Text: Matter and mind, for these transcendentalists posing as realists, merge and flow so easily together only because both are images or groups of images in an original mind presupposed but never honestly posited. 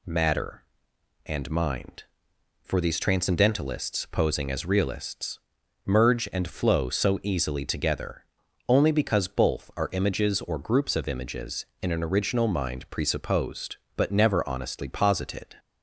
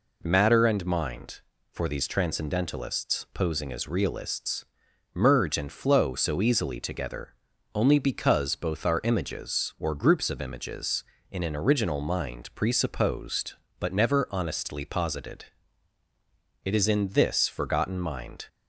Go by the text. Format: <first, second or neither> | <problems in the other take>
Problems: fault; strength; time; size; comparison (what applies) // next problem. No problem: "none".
first | pauses between "together" and "only"; at 7.3 s; 0.40 s long; also in the first // goes on to say "It is in this forgotten mind"; strong; from 16.6 s on; 1.8 s long